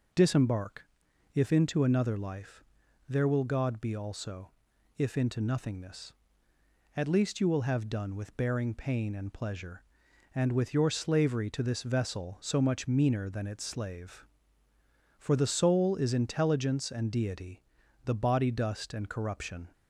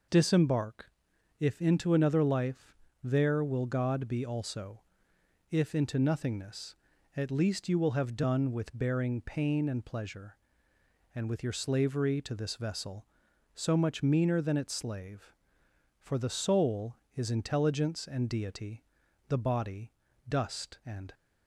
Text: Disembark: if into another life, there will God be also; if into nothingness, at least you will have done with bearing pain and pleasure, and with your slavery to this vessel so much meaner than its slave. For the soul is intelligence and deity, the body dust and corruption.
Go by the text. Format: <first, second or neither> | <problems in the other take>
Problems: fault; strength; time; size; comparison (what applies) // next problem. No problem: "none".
first | pauses between "body" and "dust"; slight; at 19.9 s; 0.36 s long // stops before "corruption"; at 21.1 s